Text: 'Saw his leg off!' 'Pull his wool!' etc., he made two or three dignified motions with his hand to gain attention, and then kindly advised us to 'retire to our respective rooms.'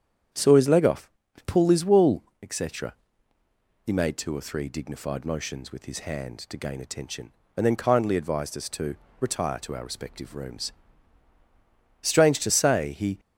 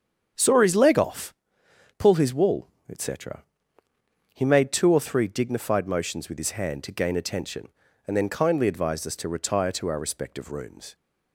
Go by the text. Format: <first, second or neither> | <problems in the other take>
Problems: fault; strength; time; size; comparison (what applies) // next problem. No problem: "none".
second | starts louder than the rest; strong; until 1.7 s; 8.5 dB; strong in the second // pauses between "to" and "retire"; slight; at 8.9 s; 0.24 s long // goes on to say "Strange to say he"; noticeable; from 12.1 s on; 1.0 s long